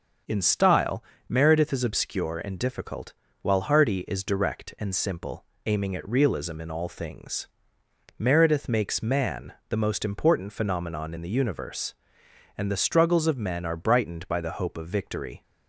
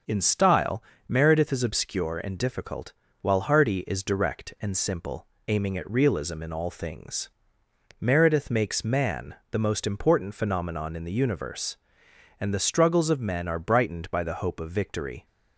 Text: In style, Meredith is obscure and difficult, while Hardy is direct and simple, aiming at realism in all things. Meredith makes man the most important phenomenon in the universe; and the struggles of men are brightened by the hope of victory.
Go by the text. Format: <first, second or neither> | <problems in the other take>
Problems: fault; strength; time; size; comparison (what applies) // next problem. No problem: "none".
neither | starts louder than the rest; the same in both // pauses between "man" and "the"; slight; the same in both